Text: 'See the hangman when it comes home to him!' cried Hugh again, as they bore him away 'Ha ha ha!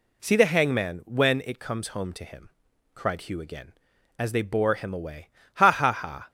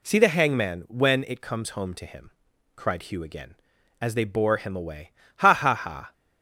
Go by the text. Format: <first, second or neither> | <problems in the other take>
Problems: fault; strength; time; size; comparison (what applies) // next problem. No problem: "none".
neither | pauses between "away" and "Ha"; slight; the same in both